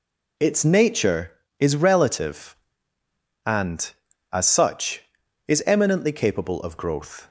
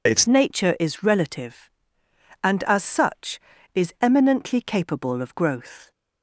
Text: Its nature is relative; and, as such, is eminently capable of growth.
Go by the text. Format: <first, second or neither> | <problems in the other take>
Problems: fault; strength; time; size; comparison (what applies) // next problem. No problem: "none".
first | changes voice at "nature"; from 0.2 s on; 5.7 s long